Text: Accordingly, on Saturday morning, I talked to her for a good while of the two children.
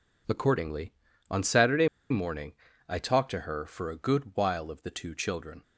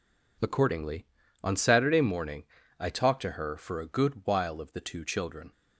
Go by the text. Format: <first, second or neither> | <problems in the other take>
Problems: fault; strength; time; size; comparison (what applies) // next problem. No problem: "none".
second | pauses between "Saturday" and "morning"; slight; at 1.8 s; 0.24 s long